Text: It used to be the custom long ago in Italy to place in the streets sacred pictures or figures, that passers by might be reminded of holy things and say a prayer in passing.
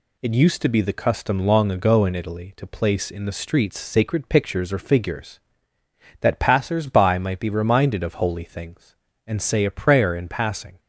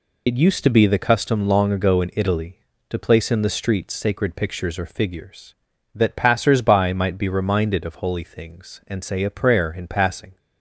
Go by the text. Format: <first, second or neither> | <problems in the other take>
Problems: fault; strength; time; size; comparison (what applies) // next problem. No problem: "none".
first | loses the start of "It"; at 0.2 s; 35 ms